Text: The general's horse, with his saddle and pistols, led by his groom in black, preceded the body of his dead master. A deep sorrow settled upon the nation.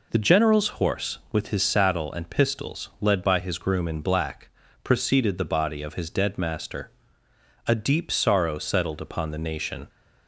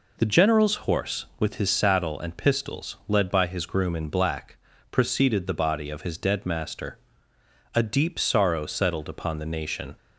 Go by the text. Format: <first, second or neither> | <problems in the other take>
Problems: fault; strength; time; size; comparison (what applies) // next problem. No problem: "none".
neither | pauses between "general's" and "horse"; slight; the same in both